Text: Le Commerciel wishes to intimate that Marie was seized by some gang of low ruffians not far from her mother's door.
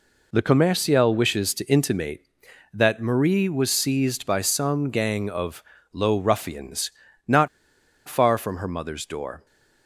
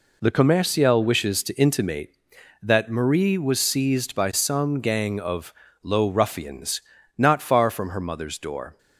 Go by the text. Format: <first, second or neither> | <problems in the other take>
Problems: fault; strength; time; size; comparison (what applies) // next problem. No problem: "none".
second | pauses between "of" and "low"; slight; at 5.6 s; 0.30 s long; slight in the second // pauses between "ruffians" and "not"; slight; at 6.9 s; 0.34 s long; slight in the second // pauses between "not" and "far"; noticeable; at 7.4 s; 0.58 s long